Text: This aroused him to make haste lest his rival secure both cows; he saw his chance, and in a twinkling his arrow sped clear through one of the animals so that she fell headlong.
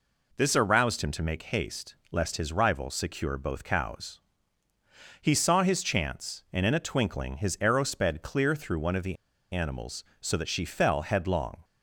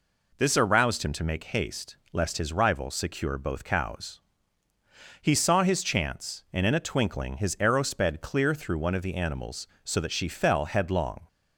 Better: second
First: pauses between "haste" and "lest"; slight; at 1.9 s; 0.16 s long // pauses between "the" and "animals"; slight; at 9.1 s; 0.36 s long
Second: pauses between "haste" and "lest"; slight; at 1.9 s; 0.16 s long

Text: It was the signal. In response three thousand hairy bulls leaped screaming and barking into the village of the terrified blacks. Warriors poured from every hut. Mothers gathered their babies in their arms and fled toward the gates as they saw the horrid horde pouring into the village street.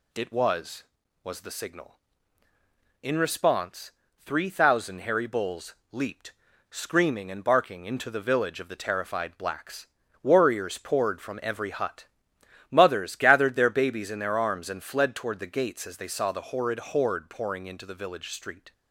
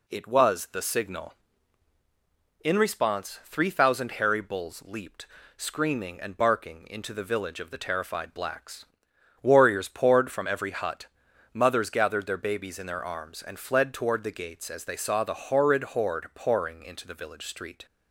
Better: second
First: says "was" twice; at 1.2 s // pauses between "response" and "three"; slight; at 3.9 s; 0.28 s long // pauses between "bulls" and "leaped"; slight; at 5.7 s; 0.16 s long // pauses between "leaped" and "screaming"; at 6.3 s; 0.37 s long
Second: pauses between "leaped" and "screaming"; slight; at 5.2 s; 0.30 s long

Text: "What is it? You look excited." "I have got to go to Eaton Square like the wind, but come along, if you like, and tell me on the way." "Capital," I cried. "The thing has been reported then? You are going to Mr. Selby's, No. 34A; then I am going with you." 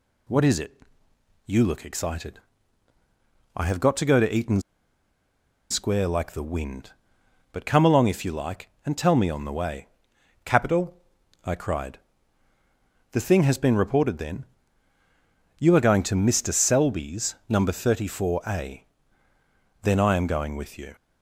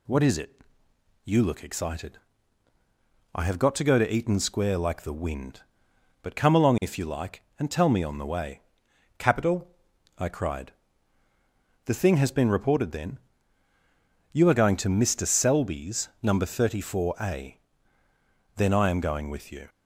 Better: second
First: pauses between "Eaton" and "Square"; at 4.6 s; 1.0 s long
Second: none

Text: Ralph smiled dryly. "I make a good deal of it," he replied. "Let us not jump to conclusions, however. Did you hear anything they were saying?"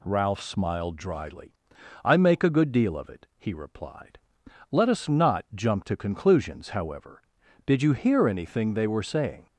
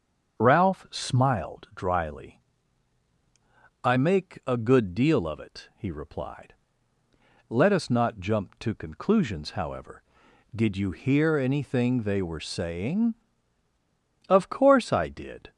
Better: first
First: none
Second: starts louder than the rest; until 1.4 s; 7 dB // goes on to say "Of course I did"; noticeable; from 14.2 s on; 1.2 s long

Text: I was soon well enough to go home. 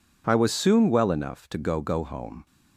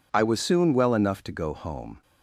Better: second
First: says "go" twice; at 1.8 s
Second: none

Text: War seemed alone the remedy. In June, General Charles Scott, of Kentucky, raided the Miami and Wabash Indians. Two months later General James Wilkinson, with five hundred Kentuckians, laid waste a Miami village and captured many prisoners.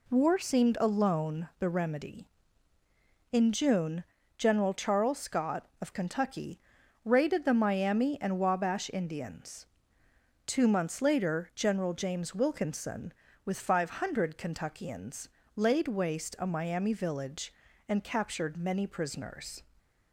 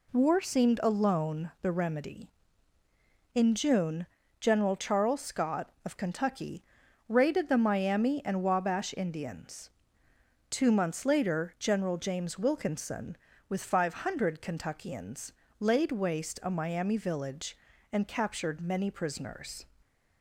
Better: neither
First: none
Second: none

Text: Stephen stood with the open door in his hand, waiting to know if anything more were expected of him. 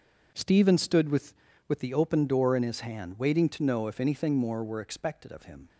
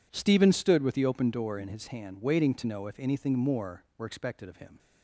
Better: second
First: says "with" twice; at 1.6 s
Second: none

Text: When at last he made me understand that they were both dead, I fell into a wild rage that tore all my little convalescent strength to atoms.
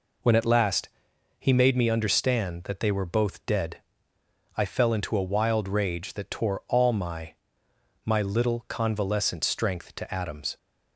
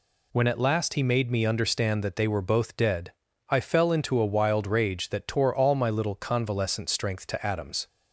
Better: second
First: pauses between "last" and "he"; noticeable; at 0.8 s; 0.50 s long // says "my" twice; at 8.0 s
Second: none

